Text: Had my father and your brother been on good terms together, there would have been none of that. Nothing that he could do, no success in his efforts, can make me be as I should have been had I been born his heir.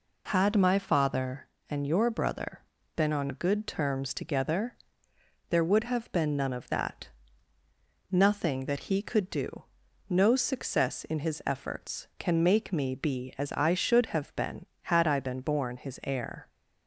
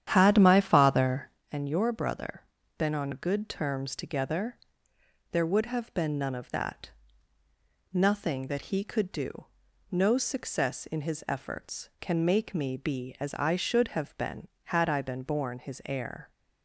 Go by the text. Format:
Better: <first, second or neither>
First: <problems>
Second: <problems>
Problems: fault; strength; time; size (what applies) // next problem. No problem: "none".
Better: first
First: pauses between "brother" and "been"; slight; at 2.6 s; 0.34 s long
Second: starts louder than the rest; strong; until 1.5 s; 10 dB // pauses between "brother" and "been"; slight; at 2.4 s; 0.34 s long